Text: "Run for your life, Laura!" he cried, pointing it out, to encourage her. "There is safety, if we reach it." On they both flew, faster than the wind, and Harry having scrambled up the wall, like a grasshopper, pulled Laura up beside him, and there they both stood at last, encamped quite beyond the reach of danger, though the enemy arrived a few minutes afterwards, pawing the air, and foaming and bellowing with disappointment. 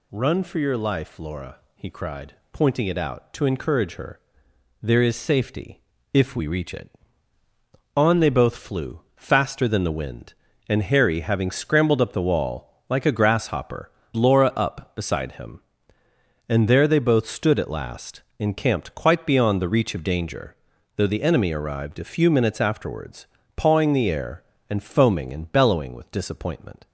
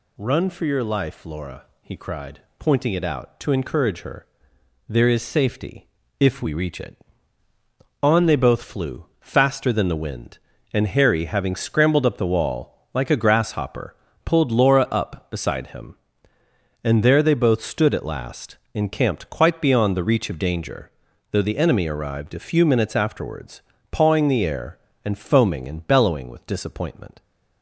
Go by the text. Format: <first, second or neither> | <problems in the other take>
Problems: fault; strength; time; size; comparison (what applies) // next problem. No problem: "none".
second | skips "pulled"; at 14.0 s